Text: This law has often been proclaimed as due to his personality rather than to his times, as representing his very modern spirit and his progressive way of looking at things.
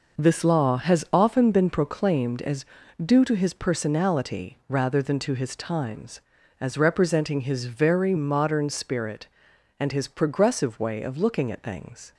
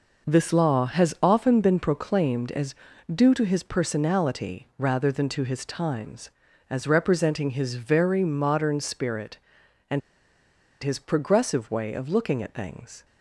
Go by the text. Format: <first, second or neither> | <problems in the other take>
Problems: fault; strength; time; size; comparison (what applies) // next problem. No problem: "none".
first | pauses between "as" and "due"; at 2.7 s; 0.40 s long; also in the first // pauses between "and" and "his"; noticeable; at 10.0 s; 0.82 s long